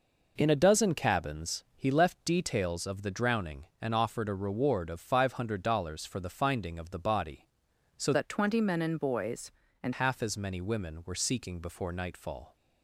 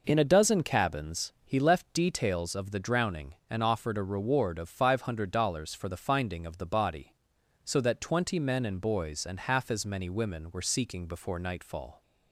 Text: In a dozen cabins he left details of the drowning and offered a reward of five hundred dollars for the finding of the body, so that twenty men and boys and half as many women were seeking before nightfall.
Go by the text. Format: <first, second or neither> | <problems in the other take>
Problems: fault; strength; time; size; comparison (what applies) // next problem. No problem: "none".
second | changes voice from "that" to "and"; from 8.1 to 9.9 s; 1.8 s long